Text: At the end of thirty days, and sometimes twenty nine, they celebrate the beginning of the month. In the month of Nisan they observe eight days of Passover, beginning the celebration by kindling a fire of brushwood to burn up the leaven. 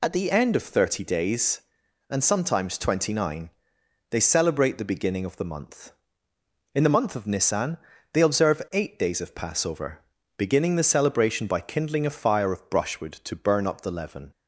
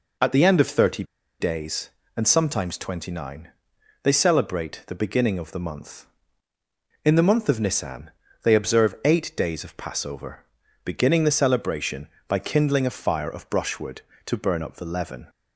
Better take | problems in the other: first | pauses between "thirty" and "days"; at 1.0 s; 0.36 s long // pauses between "Nisan" and "they"; slight; at 8.0 s; 0.34 s long; slight in the first

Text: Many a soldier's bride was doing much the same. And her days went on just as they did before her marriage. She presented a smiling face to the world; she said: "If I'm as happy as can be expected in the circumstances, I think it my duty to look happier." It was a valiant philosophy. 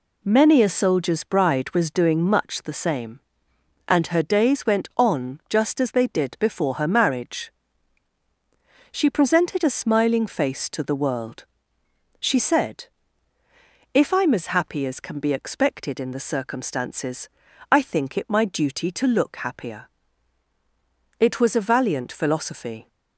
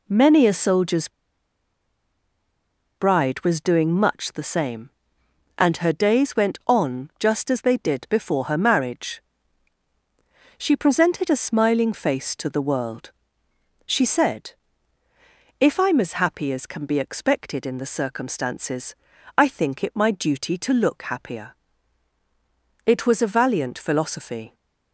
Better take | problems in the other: first | pauses between "soldier's" and "bride"; strong; at 1.0 s; 1.8 s long

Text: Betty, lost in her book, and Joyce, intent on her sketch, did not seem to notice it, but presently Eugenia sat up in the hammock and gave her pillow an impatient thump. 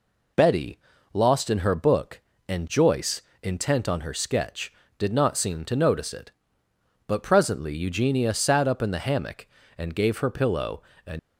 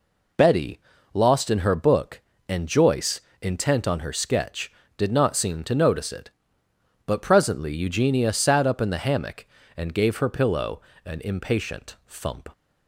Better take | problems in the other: second | pauses between "pillow" and "an"; slight; at 10.8 s; 0.24 s long; slight in the second // stops before "impatient thump"; at 11.1 s

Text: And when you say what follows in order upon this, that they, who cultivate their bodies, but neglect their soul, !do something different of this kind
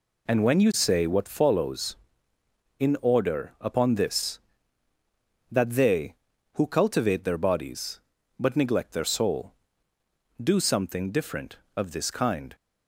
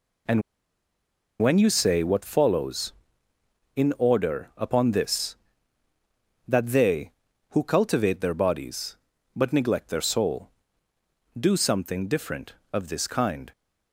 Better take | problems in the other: first | pauses between "And" and "when"; at 0.4 s; 1.0 s long

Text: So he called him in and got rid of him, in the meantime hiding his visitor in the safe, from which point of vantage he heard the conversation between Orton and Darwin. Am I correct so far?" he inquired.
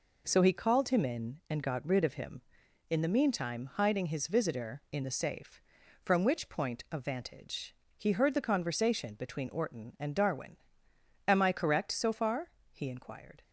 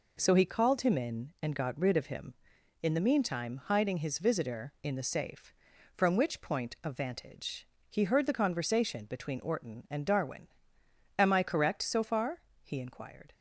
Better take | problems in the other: neither | pauses between "vantage" and "he"; slight; the same in both

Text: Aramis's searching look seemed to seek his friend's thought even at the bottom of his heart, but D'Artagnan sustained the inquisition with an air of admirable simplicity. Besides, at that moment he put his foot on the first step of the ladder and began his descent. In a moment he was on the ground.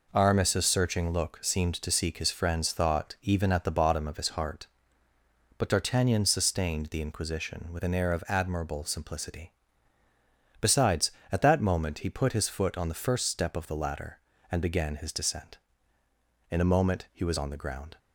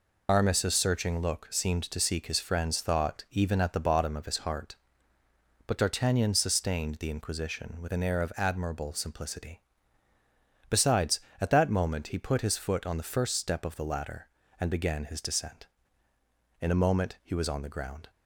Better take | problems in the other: first | loses the start of "Aramis's"; at 0.2 s; 100 ms

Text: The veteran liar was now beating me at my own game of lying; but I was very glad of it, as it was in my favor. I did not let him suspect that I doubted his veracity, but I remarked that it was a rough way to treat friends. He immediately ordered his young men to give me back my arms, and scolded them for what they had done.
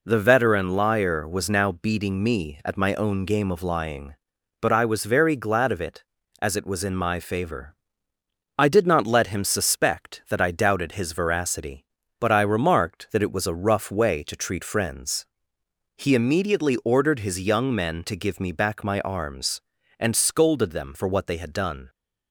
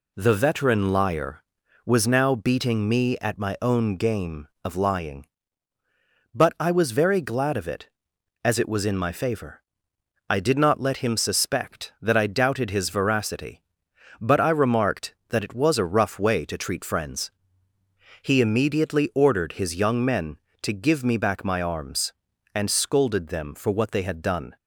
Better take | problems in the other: neither | none

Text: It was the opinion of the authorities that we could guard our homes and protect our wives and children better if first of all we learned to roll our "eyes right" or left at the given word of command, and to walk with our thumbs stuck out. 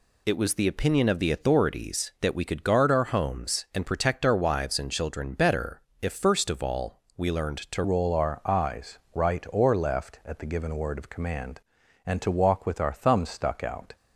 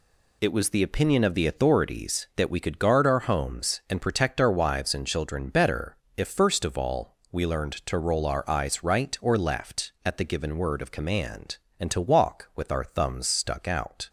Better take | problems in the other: second | pauses between "better" and "if"; slight; at 5.8 s; 0.22 s long; slight in the second // pauses between "all" and "we"; slight; at 7.0 s; 0.16 s long; slight in the second // changes voice at "roll"; from 7.8 s on; 6.1 s long

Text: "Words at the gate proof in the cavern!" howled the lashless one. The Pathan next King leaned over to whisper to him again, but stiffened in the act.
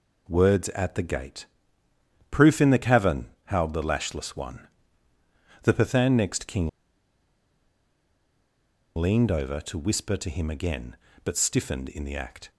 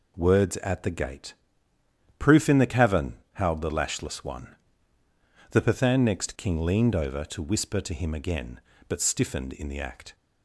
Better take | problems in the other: second | pauses between "gate" and "proof"; noticeable; at 1.4 s; 0.84 s long; noticeable in the second // pauses between "King" and "leaned"; strong; at 6.6 s; 2.2 s long

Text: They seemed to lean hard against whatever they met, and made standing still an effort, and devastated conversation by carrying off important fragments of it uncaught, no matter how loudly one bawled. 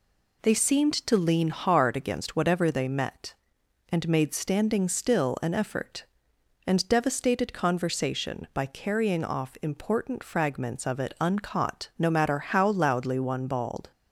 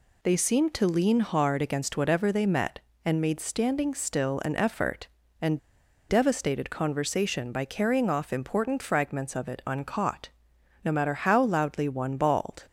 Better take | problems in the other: first | pauses between "and" and "devastated"; noticeable; at 5.5 s; 0.49 s long

